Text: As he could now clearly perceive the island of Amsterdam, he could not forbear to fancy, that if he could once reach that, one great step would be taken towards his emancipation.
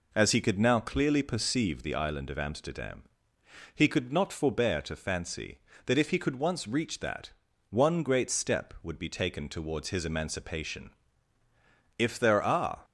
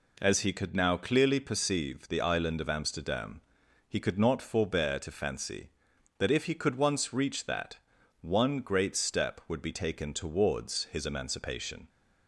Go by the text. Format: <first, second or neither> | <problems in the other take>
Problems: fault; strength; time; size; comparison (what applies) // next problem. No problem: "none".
second | goes on to say "If there are"; noticeable; from 11.9 s on; 0.86 s long